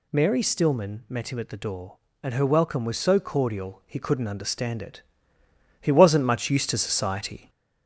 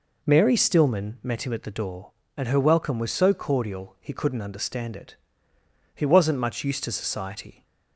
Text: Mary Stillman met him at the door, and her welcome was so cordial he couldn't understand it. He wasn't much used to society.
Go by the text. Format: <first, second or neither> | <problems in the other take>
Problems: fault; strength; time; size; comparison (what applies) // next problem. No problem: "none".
second | gets louder; slight; throughout; 3 dB